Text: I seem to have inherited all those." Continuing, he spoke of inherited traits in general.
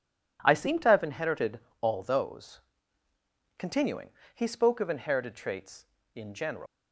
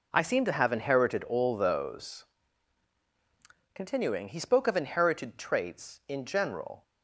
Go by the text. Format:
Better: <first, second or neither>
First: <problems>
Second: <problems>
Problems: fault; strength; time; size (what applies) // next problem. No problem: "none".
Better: second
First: pauses between "inherited" and "all"; slight; at 1.5 s; 0.22 s long // leaves "general" unfinished; at 6.6 s; 145 ms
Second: none